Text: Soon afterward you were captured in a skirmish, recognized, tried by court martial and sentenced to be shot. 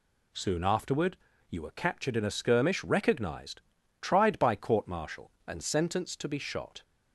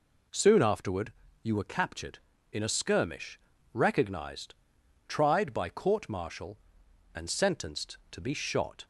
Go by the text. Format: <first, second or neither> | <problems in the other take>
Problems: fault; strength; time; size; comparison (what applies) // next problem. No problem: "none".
neither | pauses between "afterward" and "you"; slight; the same in both